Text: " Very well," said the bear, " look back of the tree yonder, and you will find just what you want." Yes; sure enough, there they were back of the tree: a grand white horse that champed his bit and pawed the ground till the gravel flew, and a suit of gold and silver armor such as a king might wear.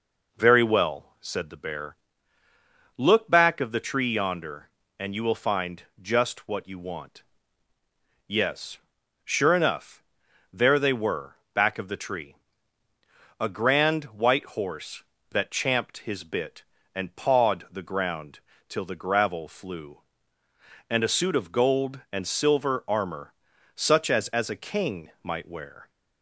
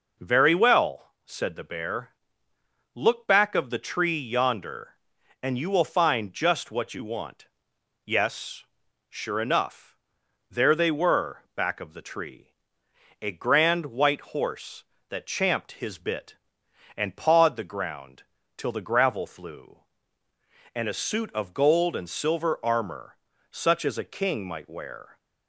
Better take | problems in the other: second | pauses between "find" and "just"; slight; at 5.8 s; 0.16 s long // pauses between "were" and "back"; slight; at 11.3 s; 0.16 s long // pauses between "ground" and "till"; slight; at 18.3 s; 0.30 s long; slight in the second // pauses between "armor" and "such"; at 23.3 s; 0.42 s long; slight in the second // says "as" twice; at 24.2 s

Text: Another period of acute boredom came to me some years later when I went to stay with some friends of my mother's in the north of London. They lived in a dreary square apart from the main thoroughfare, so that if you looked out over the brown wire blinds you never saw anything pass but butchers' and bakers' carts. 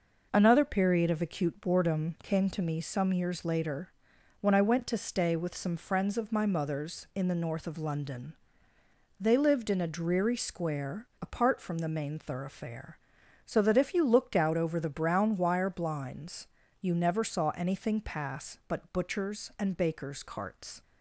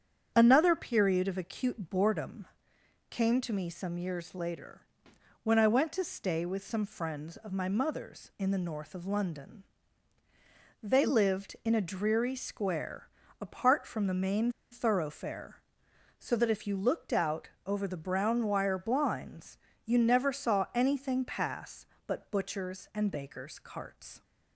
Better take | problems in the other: first | starts louder than the rest; strong; until 1.3 s; 8 dB // pauses between "boredom" and "came"; noticeable; at 2.4 s; 0.64 s long // pauses between "later" and "when"; noticeable; at 4.8 s; 0.62 s long; noticeable in the first // pauses between "square" and "apart"; slight; at 13.0 s; 0.34 s long // pauses between "main" and "thoroughfare"; slight; at 14.5 s; 0.20 s long // pauses between "out" and "over"; slight; at 17.4 s; 0.18 s long // pauses between "blinds" and "you"; slight; at 19.5 s; 0.30 s long; slight in the first

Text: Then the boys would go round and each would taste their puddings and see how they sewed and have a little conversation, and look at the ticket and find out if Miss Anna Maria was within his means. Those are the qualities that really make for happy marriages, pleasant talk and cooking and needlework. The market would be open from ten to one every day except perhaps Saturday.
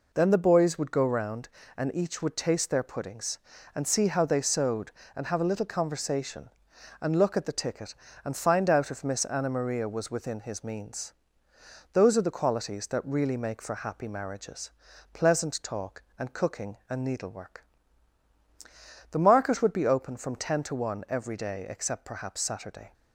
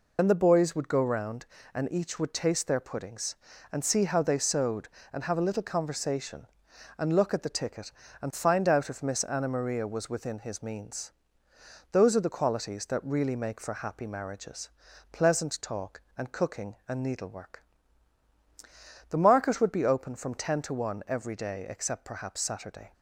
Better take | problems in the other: first | loses the start of "Then"; at 0.1 s; 80 ms

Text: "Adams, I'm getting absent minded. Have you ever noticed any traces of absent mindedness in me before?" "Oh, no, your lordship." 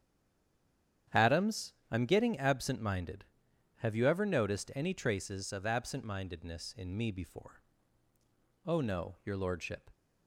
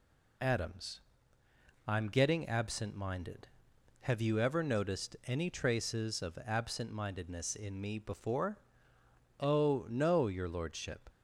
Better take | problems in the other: second | stays silent before the first word; until 1.0 s; 1.0 s long // starts louder than the rest; strong; until 2.3 s; 9.5 dB

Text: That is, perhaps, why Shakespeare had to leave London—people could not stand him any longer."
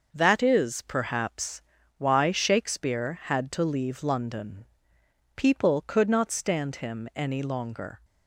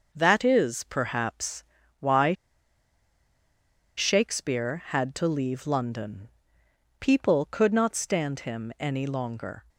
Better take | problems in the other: first | pauses between "why" and "Shakespeare"; strong; at 2.3 s; 1.6 s long

